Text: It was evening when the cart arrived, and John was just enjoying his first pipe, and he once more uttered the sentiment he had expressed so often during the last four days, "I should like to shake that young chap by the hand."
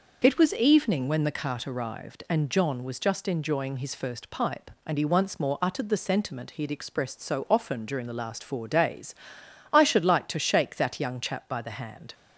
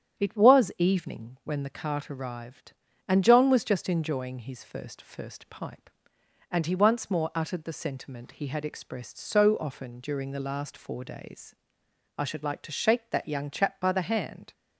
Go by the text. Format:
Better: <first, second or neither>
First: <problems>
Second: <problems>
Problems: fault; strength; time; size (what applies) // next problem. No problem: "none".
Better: first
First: none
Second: starts louder than the rest; strong; until 1.2 s; 9 dB // says "first" twice; at 4.9 s